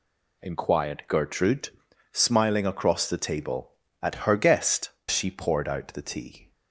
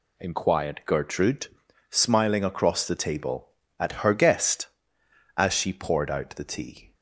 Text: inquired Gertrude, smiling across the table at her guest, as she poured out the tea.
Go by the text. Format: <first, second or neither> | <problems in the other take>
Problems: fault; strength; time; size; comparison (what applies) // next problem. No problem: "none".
second | skips "as"; at 5.0 s